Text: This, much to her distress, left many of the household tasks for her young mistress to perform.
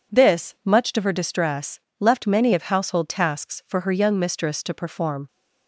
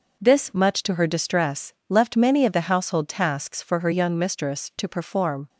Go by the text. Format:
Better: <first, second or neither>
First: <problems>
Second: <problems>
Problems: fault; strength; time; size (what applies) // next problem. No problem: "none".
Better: second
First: skips "the"; at 2.6 s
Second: none